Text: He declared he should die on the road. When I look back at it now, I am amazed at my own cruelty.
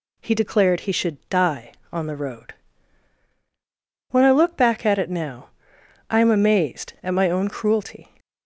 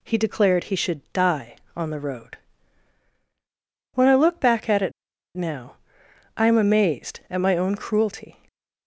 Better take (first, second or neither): first